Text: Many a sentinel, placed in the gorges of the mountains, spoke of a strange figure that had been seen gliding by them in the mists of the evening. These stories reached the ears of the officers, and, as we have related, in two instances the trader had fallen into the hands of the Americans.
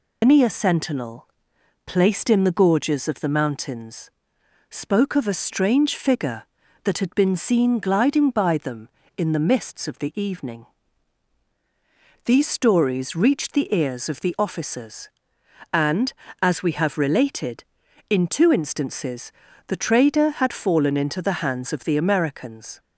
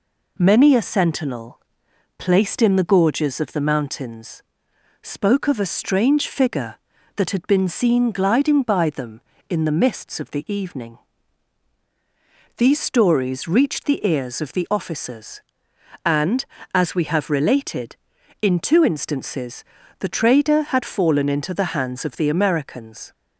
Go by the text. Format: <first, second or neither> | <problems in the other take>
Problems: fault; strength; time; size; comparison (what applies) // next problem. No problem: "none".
second | loses the start of "Many"; at 0.2 s; 180 ms // pauses between "instances" and "the"; at 19.3 s; 0.38 s long; also in the second